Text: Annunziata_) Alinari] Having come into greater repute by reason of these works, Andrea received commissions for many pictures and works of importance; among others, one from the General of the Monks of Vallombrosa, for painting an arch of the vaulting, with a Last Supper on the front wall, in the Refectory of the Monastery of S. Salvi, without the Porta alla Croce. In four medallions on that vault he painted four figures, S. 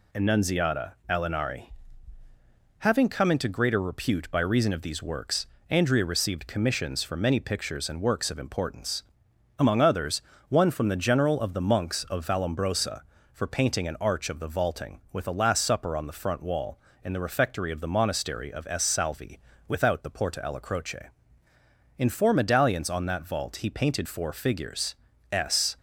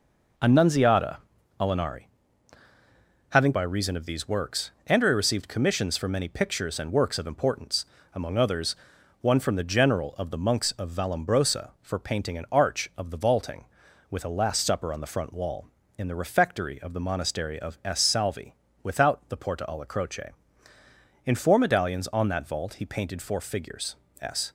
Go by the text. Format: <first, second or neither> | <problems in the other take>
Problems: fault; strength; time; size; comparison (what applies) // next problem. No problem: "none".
first | pauses between "Alinari" and "Having"; at 2.0 s; 1.2 s long; also in the first // skips "come into greater repute"; at 3.5 s